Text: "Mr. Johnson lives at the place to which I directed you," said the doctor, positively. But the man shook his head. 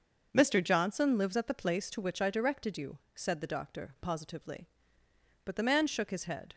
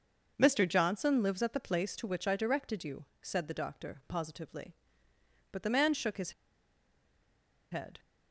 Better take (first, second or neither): first